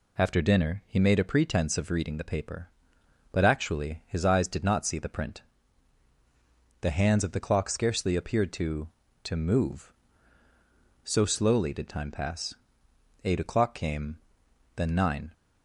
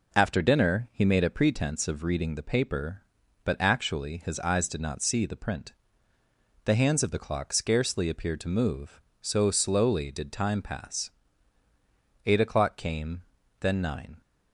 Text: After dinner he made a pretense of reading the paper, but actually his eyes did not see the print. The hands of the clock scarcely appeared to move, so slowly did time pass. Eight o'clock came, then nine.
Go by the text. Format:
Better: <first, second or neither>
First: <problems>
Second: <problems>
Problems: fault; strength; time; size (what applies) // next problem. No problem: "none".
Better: second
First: says "to" twice; at 9.2 s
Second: none